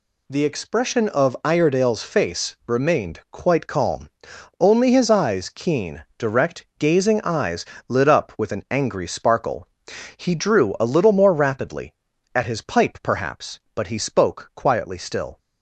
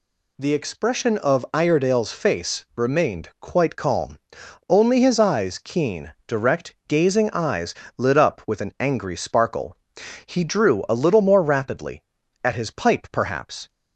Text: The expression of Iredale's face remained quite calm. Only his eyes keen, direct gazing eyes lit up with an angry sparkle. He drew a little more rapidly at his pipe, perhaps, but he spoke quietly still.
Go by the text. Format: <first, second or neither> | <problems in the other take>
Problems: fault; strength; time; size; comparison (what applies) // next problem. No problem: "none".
first | pauses between "eyes" and "lit"; slight; at 7.7 s; 0.24 s long; slight in the first // stops before "but he spoke quietly still"; at 13.6 s